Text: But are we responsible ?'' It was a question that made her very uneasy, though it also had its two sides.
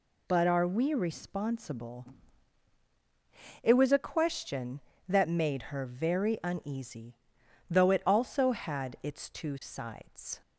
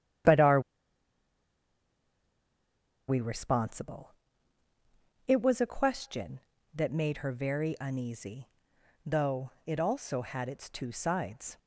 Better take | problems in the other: first | starts louder than the rest; strong; until 3.7 s; 10 dB // pauses between "are" and "we"; strong; at 0.5 s; 2.4 s long // pauses between "though" and "it"; slight; at 9.4 s; 0.16 s long

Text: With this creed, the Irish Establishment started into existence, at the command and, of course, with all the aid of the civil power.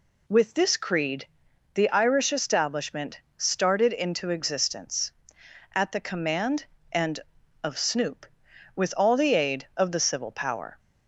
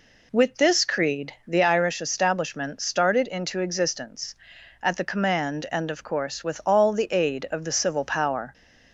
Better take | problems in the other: second | pauses between "Establishment" and "started"; slight; at 3.2 s; 0.16 s long // says "snoop" for "course"; at 7.7 s

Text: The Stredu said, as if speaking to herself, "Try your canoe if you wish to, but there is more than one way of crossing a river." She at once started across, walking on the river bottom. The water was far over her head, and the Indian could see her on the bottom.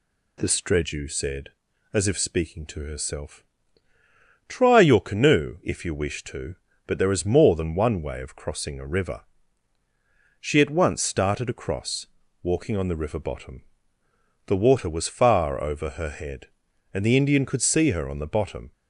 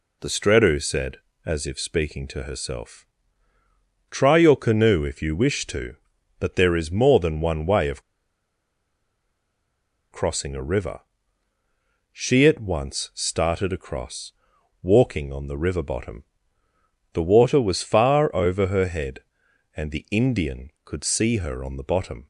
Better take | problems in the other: first | pauses between "of" and "crossing"; strong; at 8.0 s; 2.1 s long

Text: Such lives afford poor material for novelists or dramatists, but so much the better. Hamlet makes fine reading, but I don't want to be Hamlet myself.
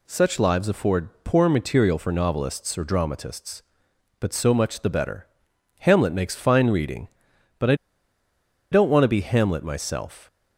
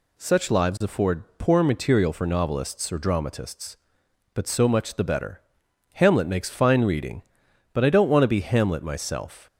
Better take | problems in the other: second | pauses between "afford" and "poor"; slight; at 1.0 s; 0.16 s long; slight in the second // pauses between "I" and "don't"; noticeable; at 7.7 s; 0.97 s long

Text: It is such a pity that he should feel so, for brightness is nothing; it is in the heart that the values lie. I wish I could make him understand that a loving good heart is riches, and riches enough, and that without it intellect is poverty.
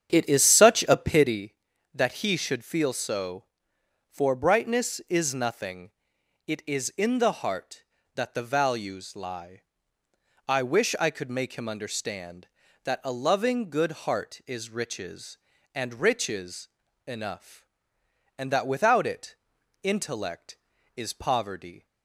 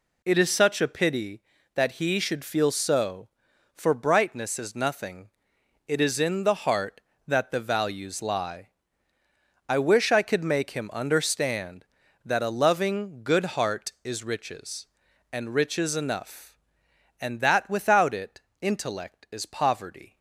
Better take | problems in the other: second | starts louder than the rest; strong; until 1.4 s; 8 dB // pauses between "riches" and "enough"; at 16.6 s; 0.40 s long // pauses between "it" and "intellect"; at 19.3 s; 0.44 s long; slight in the second

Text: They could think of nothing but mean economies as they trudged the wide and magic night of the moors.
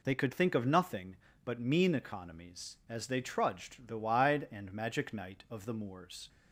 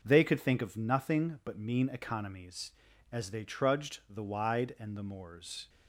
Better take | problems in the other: first | skips "magic night of"; at 4.9 s

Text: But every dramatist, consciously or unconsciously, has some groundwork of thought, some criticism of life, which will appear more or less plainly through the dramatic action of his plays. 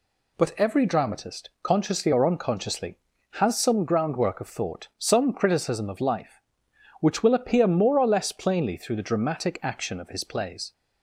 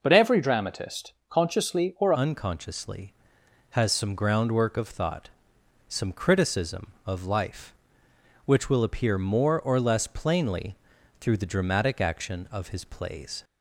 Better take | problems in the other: first | changes voice at "unconsciously"; from 2.1 s on; 11.3 s long // pauses between "plainly" and "through"; at 10.7 s; 0.44 s long

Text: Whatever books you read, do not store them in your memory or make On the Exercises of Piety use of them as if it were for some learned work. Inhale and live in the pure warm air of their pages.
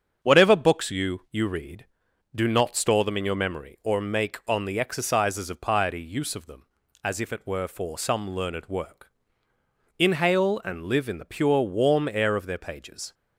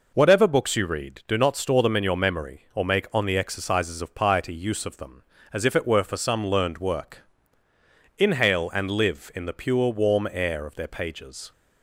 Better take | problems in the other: second | starts louder than the rest; strong; until 1.3 s; 8 dB // says "you" twice; at 1.3 s

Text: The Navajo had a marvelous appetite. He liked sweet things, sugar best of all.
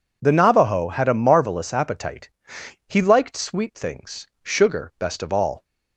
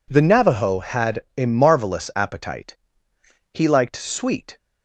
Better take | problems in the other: first | stops before "things sugar best of all"; at 4.5 s

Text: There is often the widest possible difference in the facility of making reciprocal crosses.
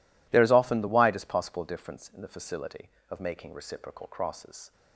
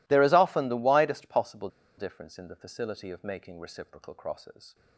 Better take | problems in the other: first | pauses between "possible" and "difference"; slight; at 1.6 s; 0.29 s long

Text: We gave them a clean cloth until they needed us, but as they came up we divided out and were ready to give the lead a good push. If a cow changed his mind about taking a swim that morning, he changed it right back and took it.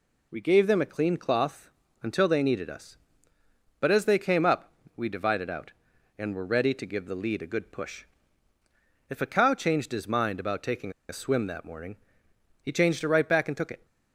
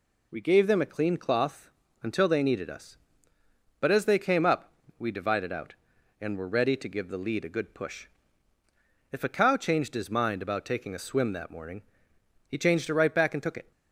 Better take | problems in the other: second | pauses between "cloth" and "until"; slight; at 1.7 s; 0.32 s long; slight in the second // pauses between "up" and "we"; slight; at 4.7 s; 0.26 s long; slight in the second // pauses between "taking" and "a"; slight; at 10.9 s; 0.18 s long

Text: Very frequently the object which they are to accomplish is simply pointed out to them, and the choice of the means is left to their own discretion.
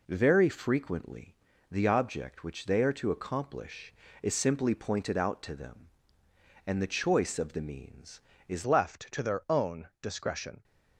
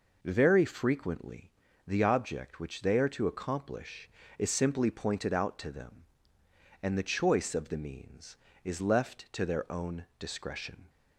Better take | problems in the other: second | pauses between "frequently" and "the"; slight; at 1.3 s; 0.36 s long; slight in the second // changes voice at "left"; from 8.6 s on; 2.0 s long

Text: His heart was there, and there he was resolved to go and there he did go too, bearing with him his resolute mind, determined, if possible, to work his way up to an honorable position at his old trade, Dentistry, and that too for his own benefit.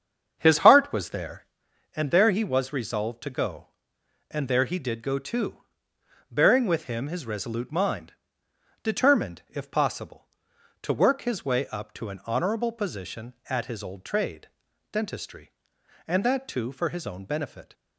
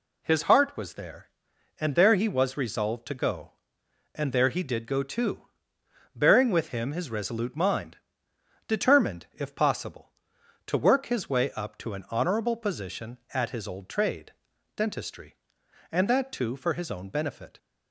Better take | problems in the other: second | starts louder than the rest; strong; until 1.6 s; 7 dB

